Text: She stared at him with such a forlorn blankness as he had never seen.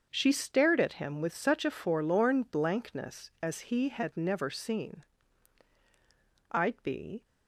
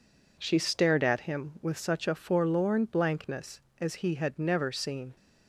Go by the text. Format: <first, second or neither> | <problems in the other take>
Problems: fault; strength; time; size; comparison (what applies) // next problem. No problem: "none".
second | starts louder than the rest; until 1.1 s; 6.5 dB // goes on to say "I'd be"; noticeable; from 6.5 s on; 0.74 s long